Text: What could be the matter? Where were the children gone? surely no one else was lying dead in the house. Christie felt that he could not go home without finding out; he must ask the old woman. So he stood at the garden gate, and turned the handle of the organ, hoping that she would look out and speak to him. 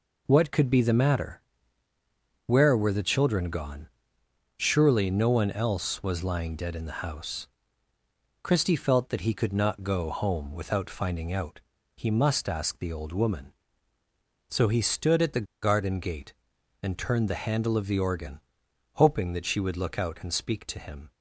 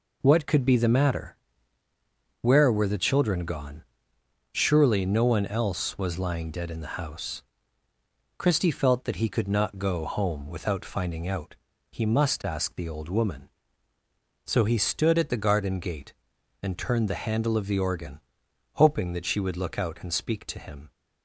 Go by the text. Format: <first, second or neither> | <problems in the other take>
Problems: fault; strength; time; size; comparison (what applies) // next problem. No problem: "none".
second | pauses between "the" and "garden"; slight; at 15.4 s; 0.17 s long